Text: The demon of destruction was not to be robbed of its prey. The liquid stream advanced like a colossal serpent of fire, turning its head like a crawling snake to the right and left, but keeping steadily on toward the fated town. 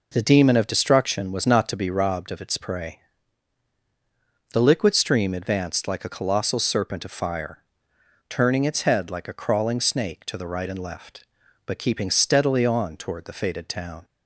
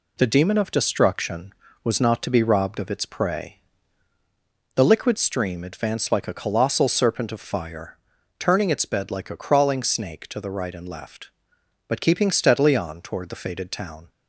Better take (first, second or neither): first